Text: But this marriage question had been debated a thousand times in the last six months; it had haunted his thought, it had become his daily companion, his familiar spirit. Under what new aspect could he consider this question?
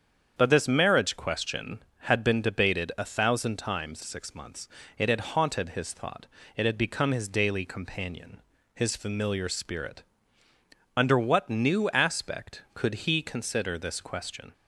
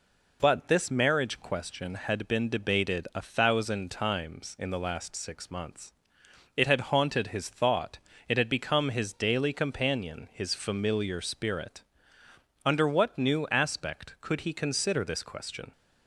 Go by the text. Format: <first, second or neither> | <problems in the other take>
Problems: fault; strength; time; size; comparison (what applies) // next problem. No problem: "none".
second | starts louder than the rest; strong; until 1.3 s; 7.5 dB // skips "in the last"; at 4.0 s